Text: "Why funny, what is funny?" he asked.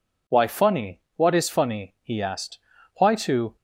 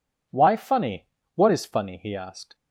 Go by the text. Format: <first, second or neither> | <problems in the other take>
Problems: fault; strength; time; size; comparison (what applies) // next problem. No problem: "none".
second | goes on to say "Why to"; from 2.9 s on; 0.60 s long